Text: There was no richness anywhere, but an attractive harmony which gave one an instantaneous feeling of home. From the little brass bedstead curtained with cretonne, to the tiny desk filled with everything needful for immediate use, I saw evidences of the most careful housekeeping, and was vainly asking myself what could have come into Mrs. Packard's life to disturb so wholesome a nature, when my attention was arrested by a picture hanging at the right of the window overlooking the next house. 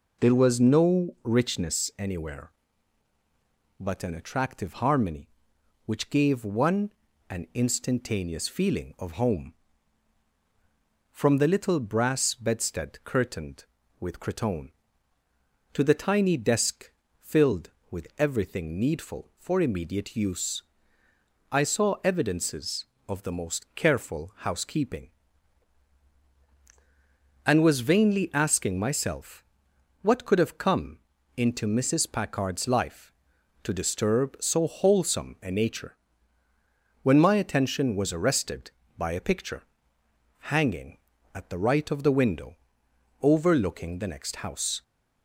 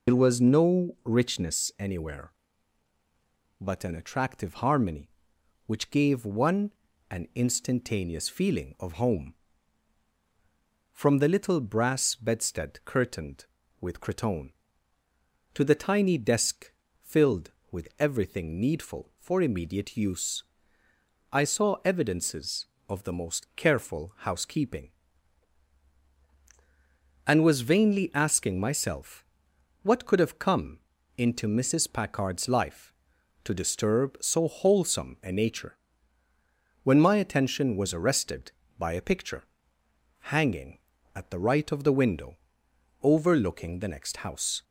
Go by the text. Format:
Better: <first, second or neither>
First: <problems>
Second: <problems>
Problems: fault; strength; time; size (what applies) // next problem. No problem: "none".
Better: first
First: pauses between "one" and "an"; at 6.9 s; 0.40 s long // pauses between "desk" and "filled"; slight; at 16.9 s; 0.32 s long // pauses between "myself" and "what"; noticeable; at 29.4 s; 0.56 s long // pauses between "come" and "into"; at 30.9 s; 0.38 s long // pauses between "picture" and "hanging"; noticeable; at 39.6 s; 0.80 s long // pauses between "window" and "overlooking"; noticeable; at 42.5 s; 0.66 s long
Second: loses the start of "There"; at 0.0 s; 65 ms // pauses between "one" and "an"; at 6.7 s; 0.40 s long // pauses between "desk" and "filled"; slight; at 16.7 s; 0.32 s long // pauses between "myself" and "what"; noticeable; at 29.2 s; 0.56 s long // pauses between "come" and "into"; at 30.7 s; 0.38 s long // pauses between "picture" and "hanging"; noticeable; at 39.4 s; 0.80 s long // pauses between "window" and "overlooking"; noticeable; at 42.3 s; 0.66 s long